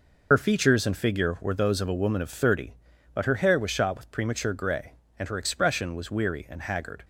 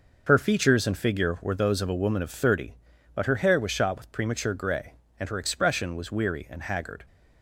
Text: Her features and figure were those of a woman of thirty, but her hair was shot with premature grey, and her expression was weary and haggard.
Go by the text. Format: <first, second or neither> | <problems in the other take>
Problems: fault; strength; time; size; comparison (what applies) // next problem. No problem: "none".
second | loses the start of "Her"; at 0.3 s; 50 ms